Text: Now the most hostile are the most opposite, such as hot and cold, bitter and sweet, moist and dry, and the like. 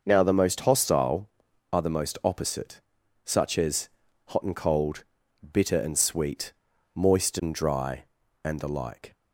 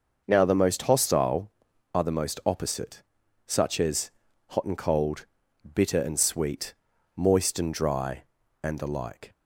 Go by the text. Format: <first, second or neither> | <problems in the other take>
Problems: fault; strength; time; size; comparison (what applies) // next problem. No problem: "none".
neither | pauses between "as" and "hot"; the same in both